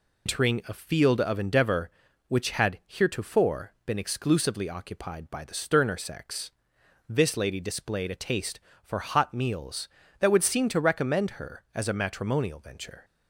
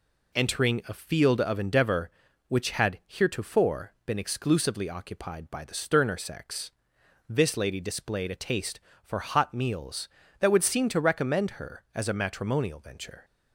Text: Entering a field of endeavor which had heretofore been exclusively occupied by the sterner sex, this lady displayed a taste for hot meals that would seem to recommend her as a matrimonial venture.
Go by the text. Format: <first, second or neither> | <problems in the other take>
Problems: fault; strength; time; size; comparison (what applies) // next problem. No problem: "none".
second | loses the start of "Entering"; at 0.2 s; 115 ms